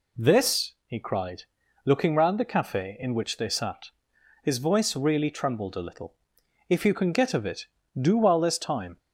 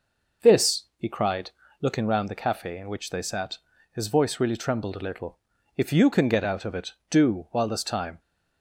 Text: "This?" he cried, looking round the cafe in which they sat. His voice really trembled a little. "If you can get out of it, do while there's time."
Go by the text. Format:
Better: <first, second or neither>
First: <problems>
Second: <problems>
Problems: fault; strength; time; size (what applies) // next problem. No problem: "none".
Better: second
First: skips "out"; at 7.3 s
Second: none